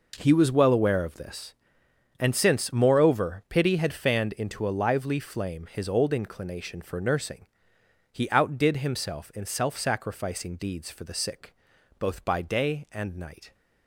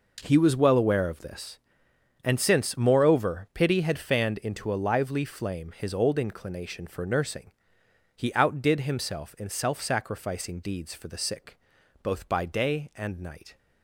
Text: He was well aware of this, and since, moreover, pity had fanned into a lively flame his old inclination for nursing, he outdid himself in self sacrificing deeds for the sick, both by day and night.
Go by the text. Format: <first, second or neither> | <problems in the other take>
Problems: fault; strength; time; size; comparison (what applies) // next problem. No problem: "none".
neither | none